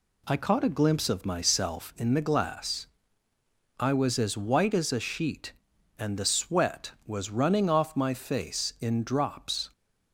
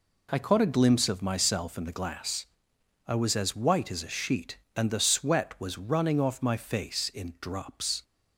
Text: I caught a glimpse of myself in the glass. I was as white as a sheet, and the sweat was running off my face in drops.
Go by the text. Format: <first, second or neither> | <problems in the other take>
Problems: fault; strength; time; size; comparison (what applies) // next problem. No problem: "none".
neither | none